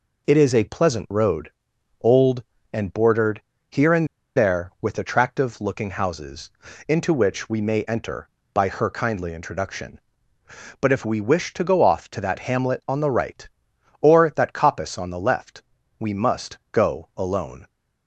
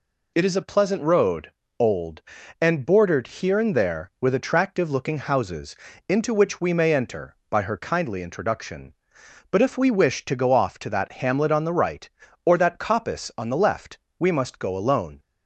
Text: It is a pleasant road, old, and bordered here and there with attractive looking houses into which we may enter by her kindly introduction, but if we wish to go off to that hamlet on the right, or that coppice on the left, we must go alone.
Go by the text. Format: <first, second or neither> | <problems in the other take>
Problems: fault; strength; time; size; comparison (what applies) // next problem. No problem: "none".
second | pauses between "bordered" and "here"; slight; at 3.4 s; 0.28 s long // pauses between "and" and "there"; slight; at 4.0 s; 0.29 s long // pauses between "houses" and "into"; at 6.4 s; 0.38 s long; slight in the second